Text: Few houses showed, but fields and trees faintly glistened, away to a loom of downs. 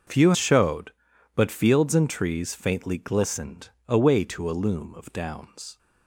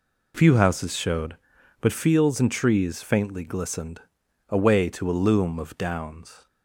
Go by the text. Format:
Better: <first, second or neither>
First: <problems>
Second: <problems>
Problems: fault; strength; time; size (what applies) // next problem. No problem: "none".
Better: second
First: starts louder than the rest; until 1.5 s; 6 dB // skips "houses"; at 0.3 s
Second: none